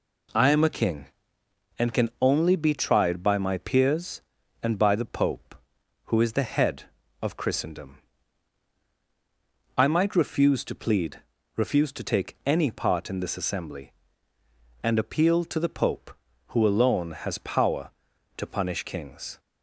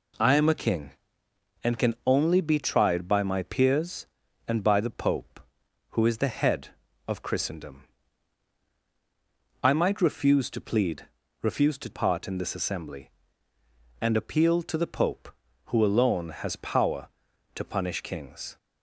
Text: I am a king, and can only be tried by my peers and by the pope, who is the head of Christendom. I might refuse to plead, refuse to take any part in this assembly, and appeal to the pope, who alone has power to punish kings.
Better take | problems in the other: first | skips "take any"; at 11.8 s

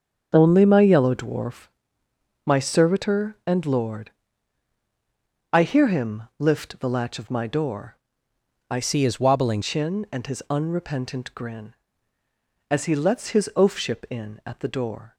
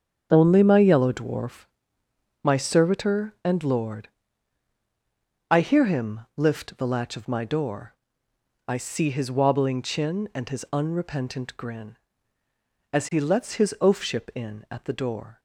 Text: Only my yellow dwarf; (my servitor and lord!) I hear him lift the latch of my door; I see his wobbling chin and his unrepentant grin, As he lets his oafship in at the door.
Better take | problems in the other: second | starts louder than the rest; strong; until 1.3 s; 7 dB; strong in the second // pauses between "him" and "lift"; slight; at 6.2 s; 0.16 s long; slight in the second // changes voice from "see" to "wobbling"; from 8.8 to 9.6 s; 0.8 s long

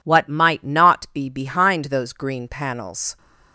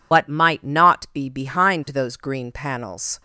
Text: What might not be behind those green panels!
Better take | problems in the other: first | loses the start of "What"; at 0.1 s; 75 ms

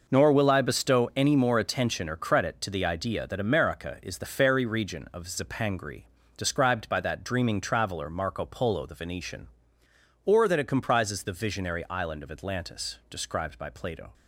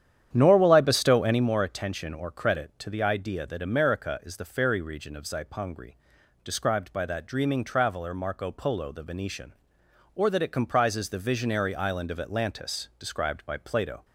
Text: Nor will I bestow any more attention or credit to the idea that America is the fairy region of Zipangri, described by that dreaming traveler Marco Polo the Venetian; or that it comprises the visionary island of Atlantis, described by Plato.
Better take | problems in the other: first | starts louder than the rest; strong; until 1.5 s; 9.5 dB

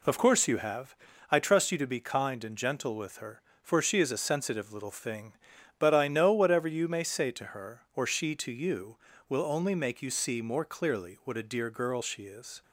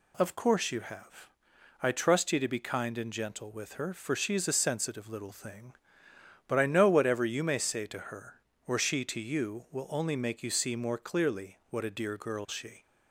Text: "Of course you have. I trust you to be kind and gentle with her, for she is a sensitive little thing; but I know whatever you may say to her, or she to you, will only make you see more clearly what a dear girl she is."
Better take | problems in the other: first | stops before "is"; at 12.8 s

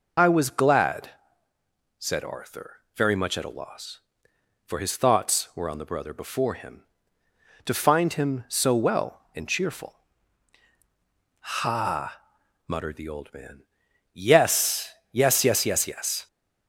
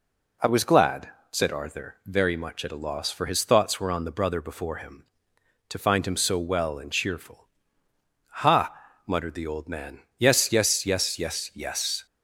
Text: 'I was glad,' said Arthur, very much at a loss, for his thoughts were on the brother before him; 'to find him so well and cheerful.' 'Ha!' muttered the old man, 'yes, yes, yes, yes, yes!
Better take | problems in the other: second | loses the start of "I"; at 0.1 s; 45 ms

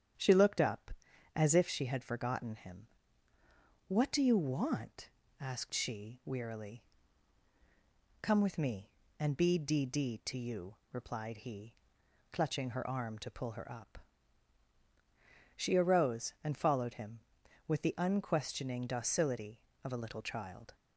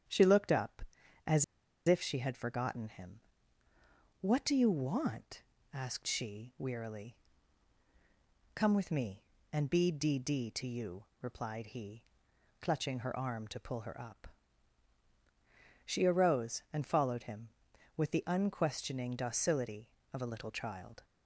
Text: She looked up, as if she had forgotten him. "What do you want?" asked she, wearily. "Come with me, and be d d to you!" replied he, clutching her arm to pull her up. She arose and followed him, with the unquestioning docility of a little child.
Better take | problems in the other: first | starts louder than the rest; strong; until 1.9 s; 9 dB; strong in the first // pauses between "as" and "if"; at 1.4 s; 0.43 s long

